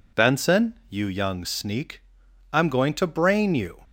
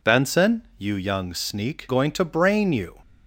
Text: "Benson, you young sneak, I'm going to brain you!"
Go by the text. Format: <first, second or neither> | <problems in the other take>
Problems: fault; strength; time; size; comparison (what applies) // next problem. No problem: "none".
first | skips "I'm"; at 1.8 s